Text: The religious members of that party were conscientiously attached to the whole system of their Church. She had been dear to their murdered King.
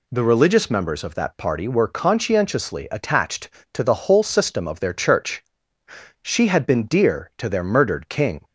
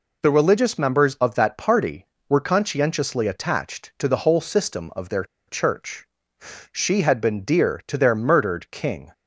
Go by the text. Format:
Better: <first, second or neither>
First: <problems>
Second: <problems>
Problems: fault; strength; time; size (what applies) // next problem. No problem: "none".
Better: first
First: none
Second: pauses between "their" and "Church"; slight; at 5.2 s; 0.23 s long